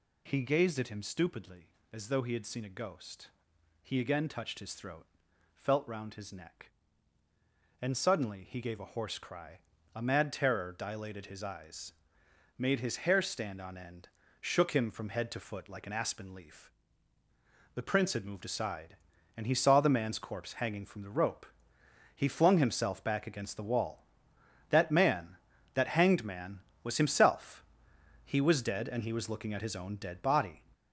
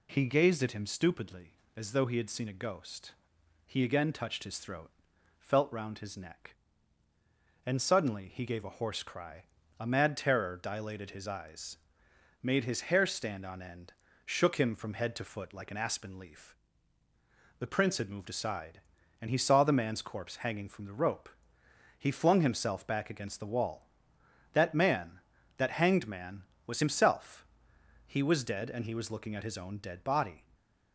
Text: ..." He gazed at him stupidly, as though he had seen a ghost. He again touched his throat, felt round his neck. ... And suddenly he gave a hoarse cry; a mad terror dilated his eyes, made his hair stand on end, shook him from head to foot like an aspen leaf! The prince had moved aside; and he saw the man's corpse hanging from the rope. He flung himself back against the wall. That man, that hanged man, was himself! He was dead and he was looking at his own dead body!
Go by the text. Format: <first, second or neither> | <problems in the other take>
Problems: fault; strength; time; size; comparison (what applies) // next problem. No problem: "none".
second | gets louder; noticeable; throughout; 6 dB